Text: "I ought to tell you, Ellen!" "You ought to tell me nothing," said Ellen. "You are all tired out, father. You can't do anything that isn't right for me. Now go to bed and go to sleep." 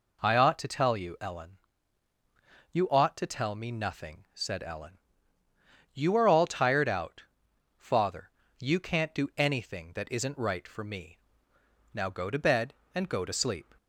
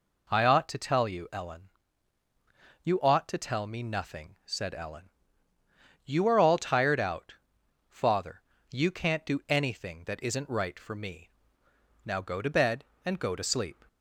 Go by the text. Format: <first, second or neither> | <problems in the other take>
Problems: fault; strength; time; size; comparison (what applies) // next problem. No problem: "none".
neither | none